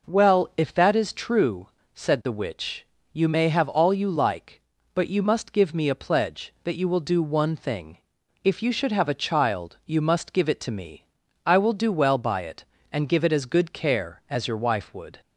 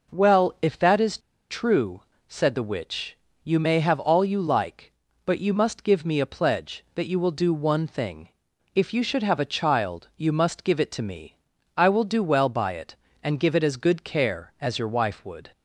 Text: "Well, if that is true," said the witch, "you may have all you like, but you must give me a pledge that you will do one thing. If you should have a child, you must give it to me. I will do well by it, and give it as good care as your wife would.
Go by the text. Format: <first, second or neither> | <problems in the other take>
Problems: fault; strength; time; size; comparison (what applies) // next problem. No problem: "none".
first | pauses between "is" and "true"; slight; at 1.1 s; 0.31 s long